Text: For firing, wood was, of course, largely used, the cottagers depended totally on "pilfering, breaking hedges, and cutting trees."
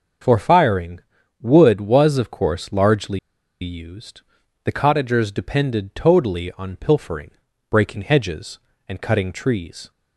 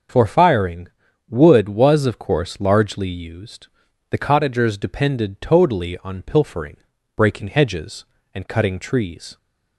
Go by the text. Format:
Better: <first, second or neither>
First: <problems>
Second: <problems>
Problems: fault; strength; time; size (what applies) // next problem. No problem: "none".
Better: second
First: starts louder than the rest; until 1.6 s; 6.5 dB // pauses between "largely" and "used"; at 3.1 s; 0.42 s long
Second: starts louder than the rest; until 1.5 s; 6.5 dB